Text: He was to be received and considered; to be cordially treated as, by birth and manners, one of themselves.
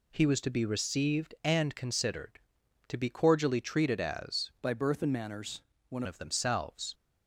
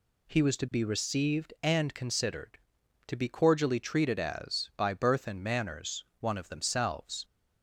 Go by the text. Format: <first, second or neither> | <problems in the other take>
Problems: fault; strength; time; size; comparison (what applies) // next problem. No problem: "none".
second | changes voice from "by" to "one"; from 4.6 to 6.0 s; 1.4 s long